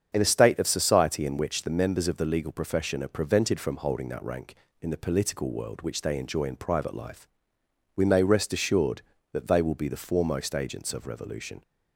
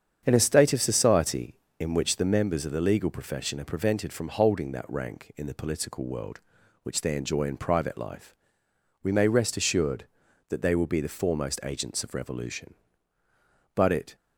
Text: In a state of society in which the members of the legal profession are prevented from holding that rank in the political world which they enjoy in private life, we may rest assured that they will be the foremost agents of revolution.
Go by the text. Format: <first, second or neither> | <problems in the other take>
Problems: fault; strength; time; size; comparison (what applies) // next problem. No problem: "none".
first | starts louder than the rest; strong; until 1.2 s; 8 dB; strong in the first // goes on to say "But it"; slight; from 13.7 s on; 0.40 s long